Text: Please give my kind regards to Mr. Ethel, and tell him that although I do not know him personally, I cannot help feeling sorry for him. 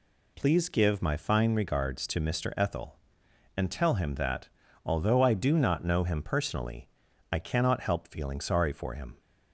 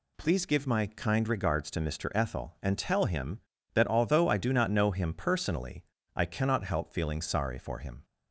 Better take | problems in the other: second | says "fine" for "kind"; at 1.1 s // pauses between "that" and "although"; at 4.4 s; 0.38 s long

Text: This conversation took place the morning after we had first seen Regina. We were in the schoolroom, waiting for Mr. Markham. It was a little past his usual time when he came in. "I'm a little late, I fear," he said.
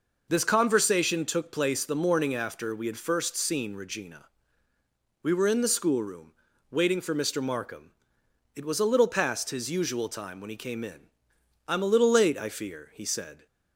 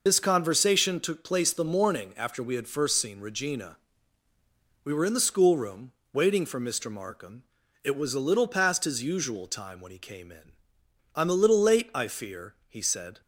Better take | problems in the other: first | loses the start of "This"; at 0.0 s; 25 ms

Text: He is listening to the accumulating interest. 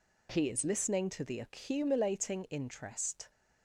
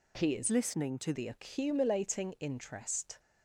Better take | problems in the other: first | changes voice from "listening" to "to"; from 0.5 to 1.1 s; 0.6 s long

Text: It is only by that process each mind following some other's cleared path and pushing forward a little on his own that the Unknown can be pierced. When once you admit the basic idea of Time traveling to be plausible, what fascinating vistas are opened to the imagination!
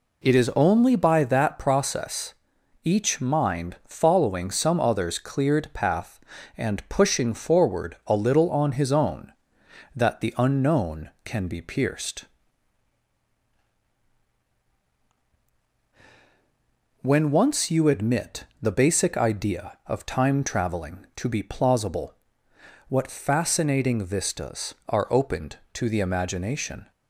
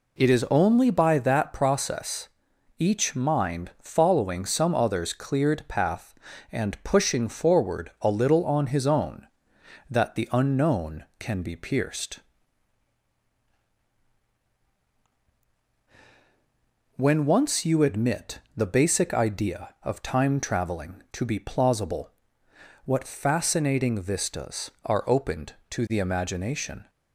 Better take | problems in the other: neither | pauses between "process" and "each"; noticeable; the same in both // pauses between "admit" and "the"; slight; the same in both

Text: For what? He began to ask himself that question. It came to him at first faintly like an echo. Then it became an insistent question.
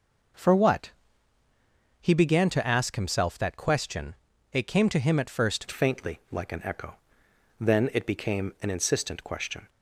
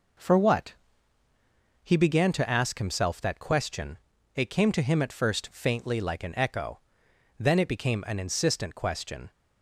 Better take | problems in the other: second | changes voice at "faintly"; from 5.7 s on; 3.9 s long

